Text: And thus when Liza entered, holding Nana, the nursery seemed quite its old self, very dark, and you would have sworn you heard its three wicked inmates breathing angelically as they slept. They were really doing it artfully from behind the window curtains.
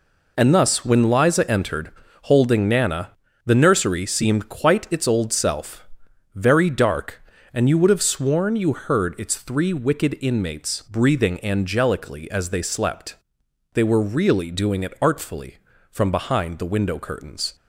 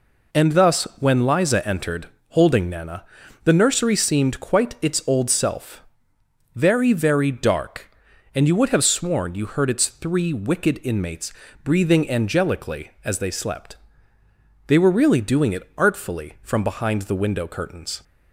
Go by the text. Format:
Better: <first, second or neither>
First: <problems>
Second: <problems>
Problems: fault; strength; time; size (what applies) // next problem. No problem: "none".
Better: first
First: none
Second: says "very" twice; at 6.9 s // pauses between "inmates" and "breathing"; slight; at 11.3 s; 0.30 s long